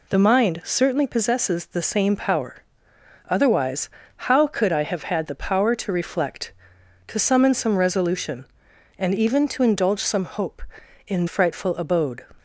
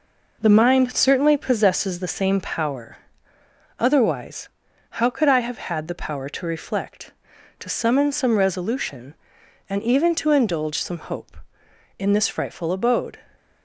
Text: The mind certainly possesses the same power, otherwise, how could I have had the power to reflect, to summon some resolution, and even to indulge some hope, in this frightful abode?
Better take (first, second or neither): second